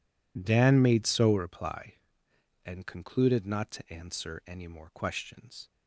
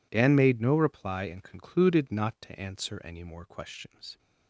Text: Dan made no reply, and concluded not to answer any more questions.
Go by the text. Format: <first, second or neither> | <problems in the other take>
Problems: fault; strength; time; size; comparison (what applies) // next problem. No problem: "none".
second | says "so" for "no"; at 1.0 s